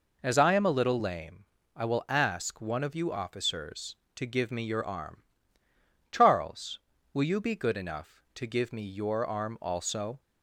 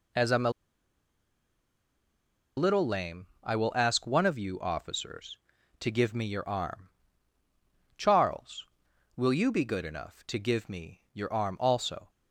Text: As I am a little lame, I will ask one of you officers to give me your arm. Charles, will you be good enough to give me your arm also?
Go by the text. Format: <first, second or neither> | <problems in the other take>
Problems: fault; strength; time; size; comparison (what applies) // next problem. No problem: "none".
first | pauses between "a" and "little"; strong; at 0.5 s; 2.0 s long